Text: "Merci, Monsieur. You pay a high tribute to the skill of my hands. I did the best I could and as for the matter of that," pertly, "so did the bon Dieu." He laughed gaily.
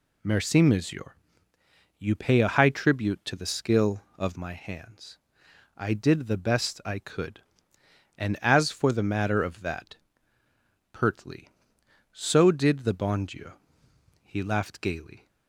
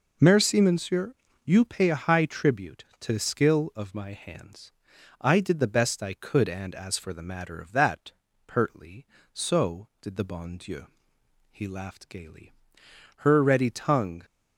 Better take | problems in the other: first | goes on to say "Her ready tongue"; noticeable; from 13.2 s on; 0.96 s long

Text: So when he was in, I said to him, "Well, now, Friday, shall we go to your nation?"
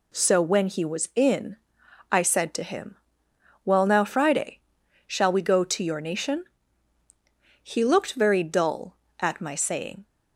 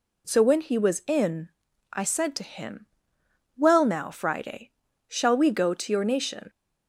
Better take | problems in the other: second | goes on to say "He looked very dull at my saying"; strong; from 7.6 s on; 2.4 s long

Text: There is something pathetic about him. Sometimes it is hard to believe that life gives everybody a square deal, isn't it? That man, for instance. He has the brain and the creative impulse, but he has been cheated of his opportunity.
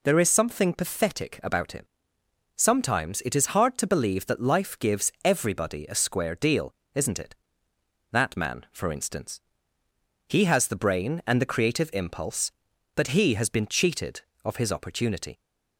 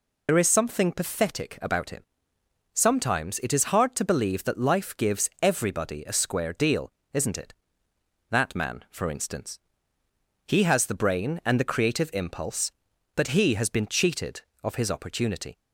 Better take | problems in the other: first | loses the start of "There"; at 0.2 s; 60 ms

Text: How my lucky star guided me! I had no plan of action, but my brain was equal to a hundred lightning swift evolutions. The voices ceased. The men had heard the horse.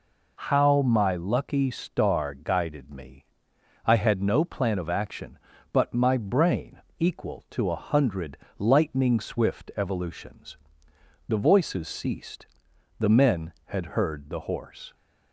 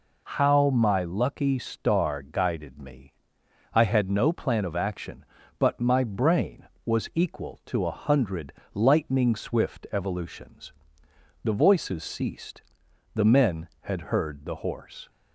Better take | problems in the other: second | skips "was"; at 6.8 s // pauses between "hundred" and "lightning"; slight; at 8.3 s; 0.22 s long; slight in the second

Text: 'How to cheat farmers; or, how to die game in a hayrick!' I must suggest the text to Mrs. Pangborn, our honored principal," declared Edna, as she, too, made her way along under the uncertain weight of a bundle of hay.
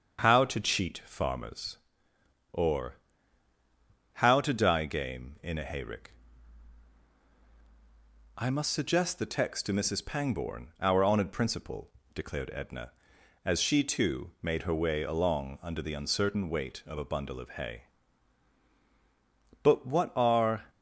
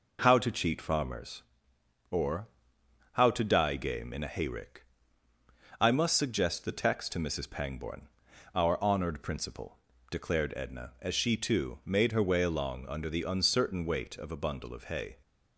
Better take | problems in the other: second | starts louder than the rest; strong; until 1.2 s; 7 dB // goes on to say "But what are"; noticeable; from 19.6 s on; 1.0 s long

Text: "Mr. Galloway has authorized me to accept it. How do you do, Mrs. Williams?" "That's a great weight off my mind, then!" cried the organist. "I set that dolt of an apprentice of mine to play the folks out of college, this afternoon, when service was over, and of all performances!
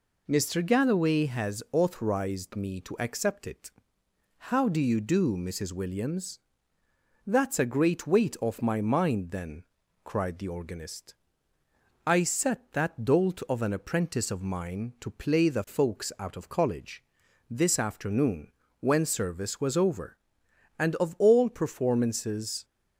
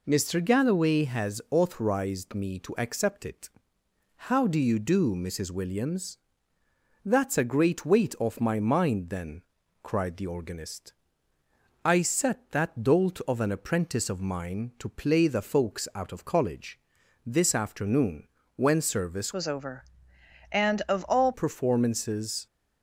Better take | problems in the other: first | changes voice from "was" to "all"; from 19.3 to 21.3 s; 2.0 s long

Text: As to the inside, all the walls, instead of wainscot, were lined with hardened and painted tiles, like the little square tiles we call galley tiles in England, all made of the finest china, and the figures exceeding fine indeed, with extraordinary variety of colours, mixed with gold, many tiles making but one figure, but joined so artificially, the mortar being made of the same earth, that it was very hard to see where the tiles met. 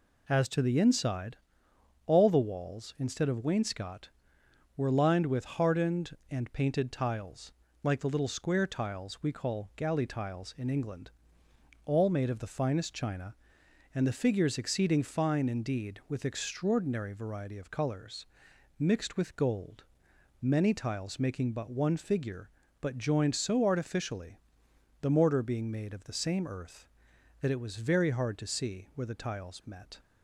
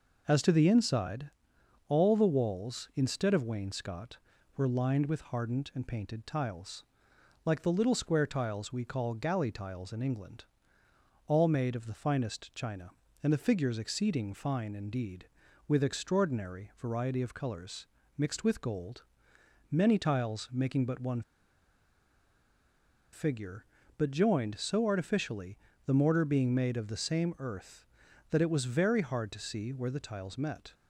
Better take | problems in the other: first | pauses between "one" and "figure"; strong; at 21.2 s; 1.9 s long

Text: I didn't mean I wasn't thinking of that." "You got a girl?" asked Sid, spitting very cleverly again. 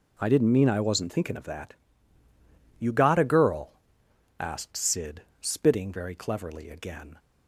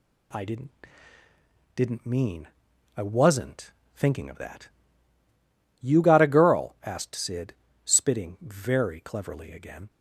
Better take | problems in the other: first | says "didn't" twice; at 1.7 s // pauses between "mean" and "I"; noticeable; at 2.4 s; 0.48 s long // pauses between "wasn't" and "thinking"; slight; at 3.7 s; 0.22 s long

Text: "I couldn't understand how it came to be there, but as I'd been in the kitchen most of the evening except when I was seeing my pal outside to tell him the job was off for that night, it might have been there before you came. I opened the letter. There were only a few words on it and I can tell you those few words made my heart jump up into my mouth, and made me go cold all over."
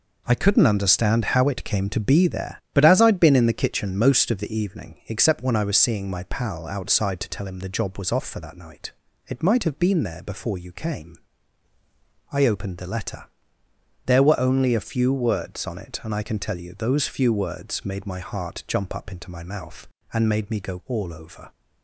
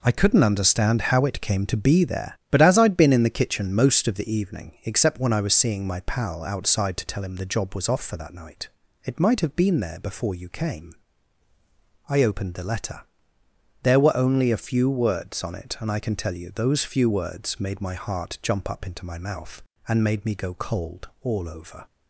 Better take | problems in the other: second | skips "cold"; at 20.8 s

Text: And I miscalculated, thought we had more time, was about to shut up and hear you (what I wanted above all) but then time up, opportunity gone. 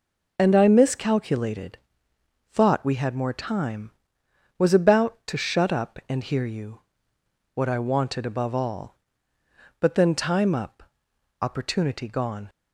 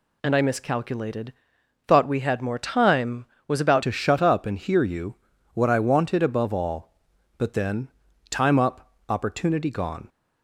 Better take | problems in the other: first | changes voice at "to"; from 3.8 s on; 6.2 s long // pauses between "then" and "time"; at 7.8 s; 0.42 s long

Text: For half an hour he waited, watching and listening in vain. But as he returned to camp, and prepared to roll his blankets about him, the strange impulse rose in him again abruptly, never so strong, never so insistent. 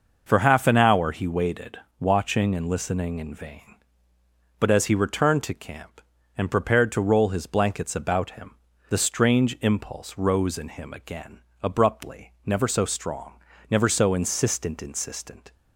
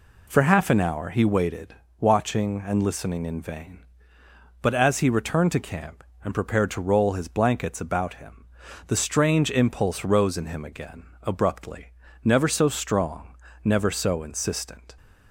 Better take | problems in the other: second | pauses between "again" and "abruptly"; slight; at 11.4 s; 0.20 s long; slight in the second // says "insistent" twice; at 14.8 s

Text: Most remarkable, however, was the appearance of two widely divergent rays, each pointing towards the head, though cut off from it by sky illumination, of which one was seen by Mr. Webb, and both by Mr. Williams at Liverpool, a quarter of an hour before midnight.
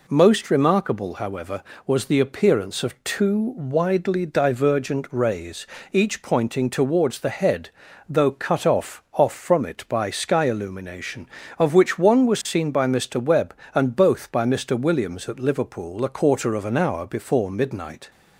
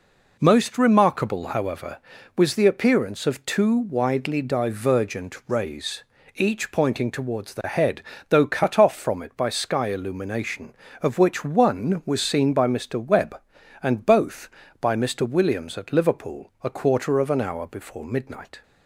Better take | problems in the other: second | says "off" twice; at 9.1 s

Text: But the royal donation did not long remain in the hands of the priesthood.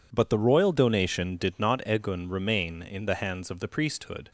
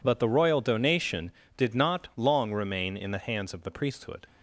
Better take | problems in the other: second | says "egun" for "long"; at 1.8 s

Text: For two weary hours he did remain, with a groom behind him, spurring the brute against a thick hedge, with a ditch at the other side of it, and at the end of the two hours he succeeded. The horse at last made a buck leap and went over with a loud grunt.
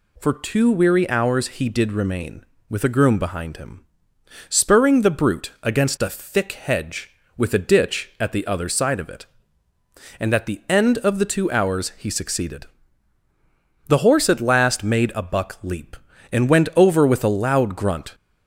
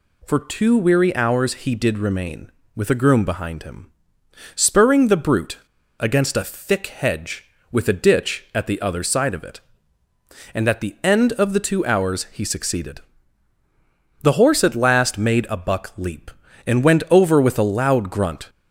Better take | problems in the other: first | pauses between "brute" and "against"; at 5.5 s; 0.42 s long

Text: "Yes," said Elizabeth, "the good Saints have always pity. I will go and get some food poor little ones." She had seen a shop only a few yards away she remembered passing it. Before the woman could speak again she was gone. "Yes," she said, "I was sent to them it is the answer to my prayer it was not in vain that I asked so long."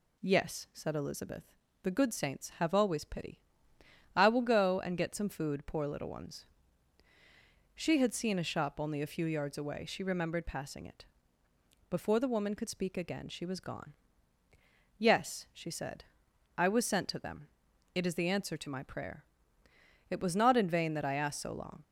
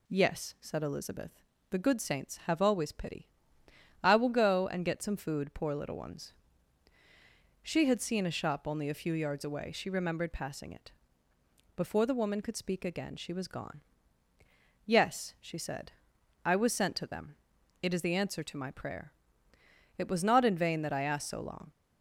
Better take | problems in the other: neither | pauses between "them" and "it"; the same in both // pauses between "prayer" and "it"; noticeable; the same in both

